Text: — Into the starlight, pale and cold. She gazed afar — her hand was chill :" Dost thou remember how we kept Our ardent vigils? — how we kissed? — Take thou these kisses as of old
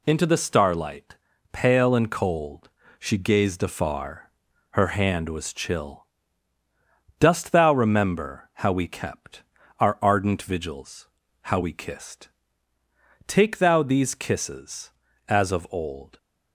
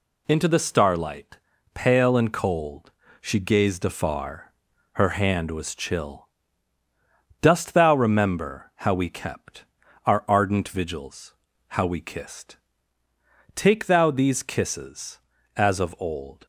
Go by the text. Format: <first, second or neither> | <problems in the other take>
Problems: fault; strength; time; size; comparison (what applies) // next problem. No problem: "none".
neither | pauses between "kept" and "Our"; the same in both